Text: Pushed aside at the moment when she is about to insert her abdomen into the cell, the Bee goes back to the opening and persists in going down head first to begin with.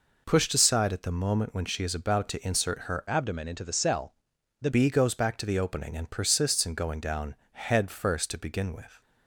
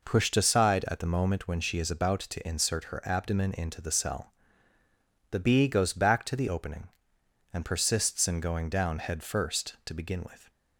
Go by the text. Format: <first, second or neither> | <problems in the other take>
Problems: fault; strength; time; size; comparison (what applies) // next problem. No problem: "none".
second | changes voice from "abdomen" to "the"; from 3.0 to 4.6 s; 1.6 s long // pauses between "down" and "head"; slight; at 7.3 s; 0.18 s long